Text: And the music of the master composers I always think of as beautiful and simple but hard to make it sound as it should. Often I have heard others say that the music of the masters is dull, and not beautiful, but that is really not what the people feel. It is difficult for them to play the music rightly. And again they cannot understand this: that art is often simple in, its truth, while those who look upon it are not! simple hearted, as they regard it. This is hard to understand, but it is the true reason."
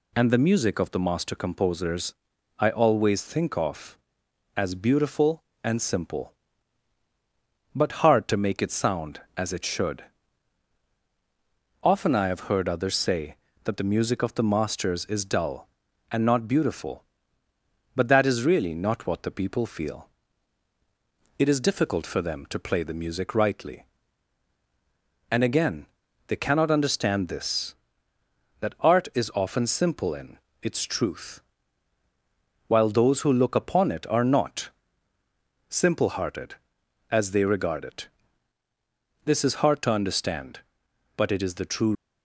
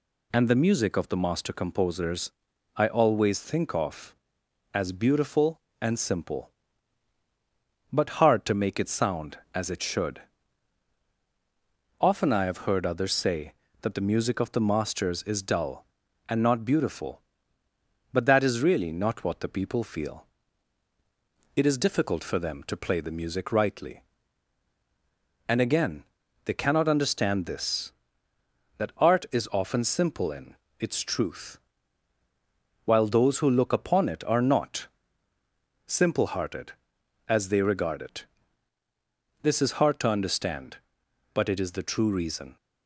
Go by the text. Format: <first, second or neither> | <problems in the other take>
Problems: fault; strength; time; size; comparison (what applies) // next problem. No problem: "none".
second | pauses between "composers" and "I"; noticeable; at 2.1 s; 0.46 s long; noticeable in the second // pauses between "again" and "they"; at 25.8 s; 0.40 s long; also in the second // stops before "reason"; at 41.9 s